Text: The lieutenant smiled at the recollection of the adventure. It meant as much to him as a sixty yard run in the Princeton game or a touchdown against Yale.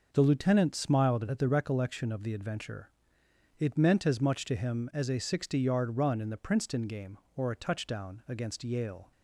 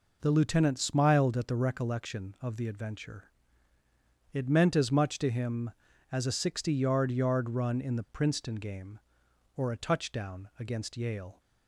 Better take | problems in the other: first | says "yard" twice; at 7.1 s

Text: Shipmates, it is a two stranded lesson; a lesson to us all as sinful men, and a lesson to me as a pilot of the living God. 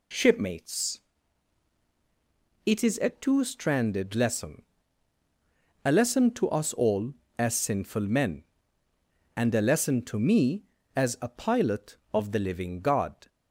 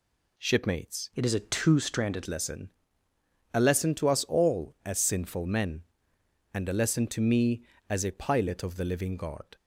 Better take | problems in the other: first | changes voice from "it" to "stranded"; from 1.1 to 2.2 s; 1.1 s long

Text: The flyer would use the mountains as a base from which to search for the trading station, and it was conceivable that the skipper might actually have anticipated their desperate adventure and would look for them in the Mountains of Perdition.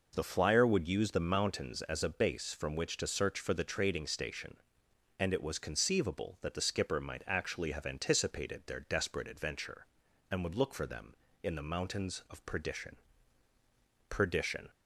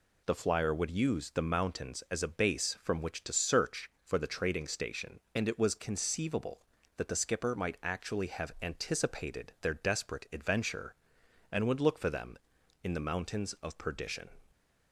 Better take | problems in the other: second | says "Perdition" twice; at 14.0 s

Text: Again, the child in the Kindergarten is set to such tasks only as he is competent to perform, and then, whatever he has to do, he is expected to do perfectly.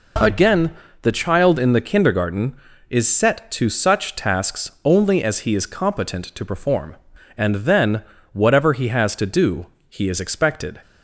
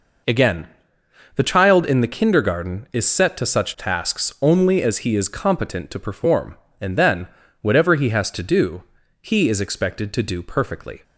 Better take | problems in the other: second | stops before "to do perfectly"; at 10.8 s

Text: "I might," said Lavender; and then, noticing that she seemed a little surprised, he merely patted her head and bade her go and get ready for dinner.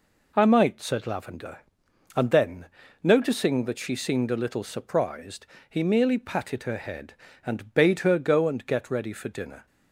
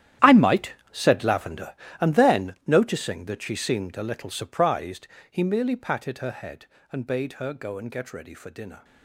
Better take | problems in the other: first | gets quieter; strong; throughout; 15 dB

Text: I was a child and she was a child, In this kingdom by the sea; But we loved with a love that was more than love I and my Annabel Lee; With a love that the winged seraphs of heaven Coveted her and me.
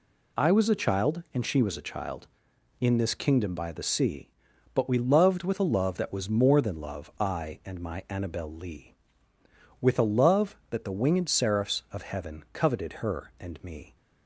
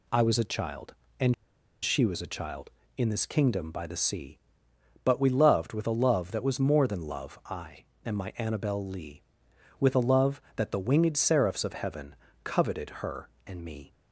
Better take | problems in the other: first | pauses between "and" and "she"; noticeable; at 1.3 s; 0.49 s long // pauses between "heaven" and "Coveted"; slight; at 12.1 s; 0.30 s long

